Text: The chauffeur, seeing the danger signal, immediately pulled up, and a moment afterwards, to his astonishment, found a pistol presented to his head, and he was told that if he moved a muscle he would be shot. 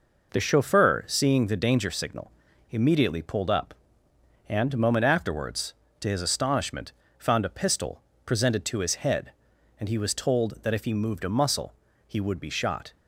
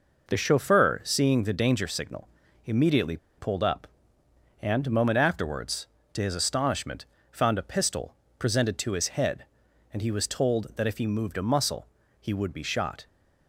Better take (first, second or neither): first